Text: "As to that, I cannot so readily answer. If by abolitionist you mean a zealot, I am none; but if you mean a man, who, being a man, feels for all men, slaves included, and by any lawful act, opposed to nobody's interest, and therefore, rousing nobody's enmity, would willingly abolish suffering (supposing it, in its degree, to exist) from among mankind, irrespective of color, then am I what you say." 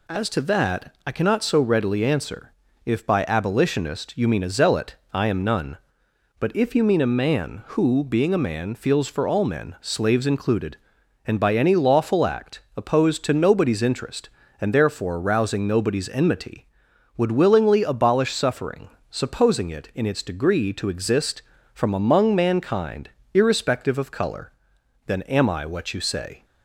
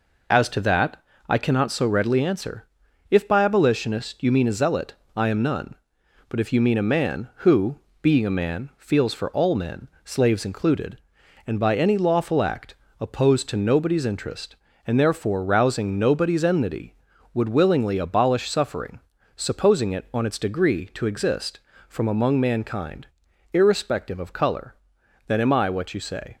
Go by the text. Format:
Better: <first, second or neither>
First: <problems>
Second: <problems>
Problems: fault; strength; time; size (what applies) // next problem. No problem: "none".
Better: first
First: none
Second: says "on" for "in"; at 20.1 s